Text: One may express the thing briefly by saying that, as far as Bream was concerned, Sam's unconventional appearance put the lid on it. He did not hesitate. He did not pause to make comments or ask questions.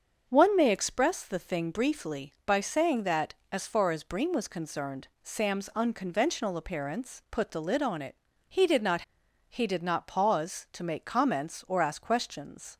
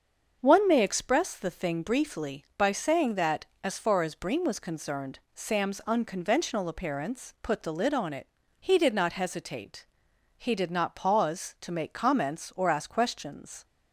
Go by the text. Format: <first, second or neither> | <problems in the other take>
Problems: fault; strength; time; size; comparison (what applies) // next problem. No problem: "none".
second | starts louder than the rest; until 1.3 s; 6.5 dB; also in the second // skips "hesitate"; at 9.2 s